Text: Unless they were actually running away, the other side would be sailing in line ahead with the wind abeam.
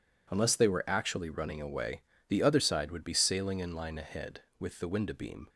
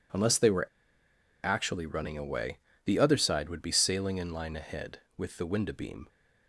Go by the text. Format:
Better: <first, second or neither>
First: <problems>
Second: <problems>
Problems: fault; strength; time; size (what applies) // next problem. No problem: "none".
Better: first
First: none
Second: pauses between "were" and "actually"; noticeable; at 0.6 s; 0.76 s long